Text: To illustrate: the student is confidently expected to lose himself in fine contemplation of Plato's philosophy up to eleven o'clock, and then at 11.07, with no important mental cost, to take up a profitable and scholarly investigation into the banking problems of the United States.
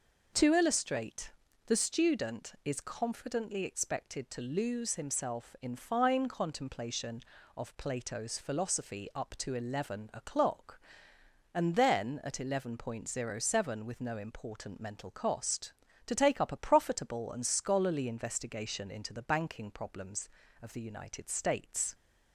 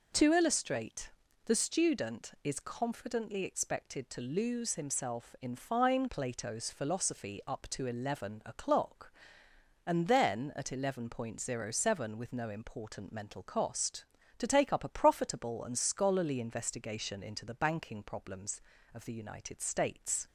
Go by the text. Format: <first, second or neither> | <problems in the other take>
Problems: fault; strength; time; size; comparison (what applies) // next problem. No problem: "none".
first | skips "contemplation of"; at 6.0 s